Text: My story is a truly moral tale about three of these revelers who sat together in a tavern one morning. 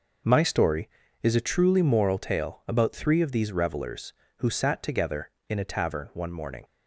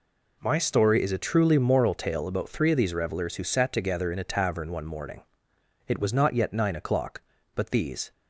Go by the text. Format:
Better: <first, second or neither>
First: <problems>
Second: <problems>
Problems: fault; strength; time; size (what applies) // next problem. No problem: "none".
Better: first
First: none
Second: goes on to say "It was not yet nine o'clock but these"; strong; from 5.8 s on; 2.2 s long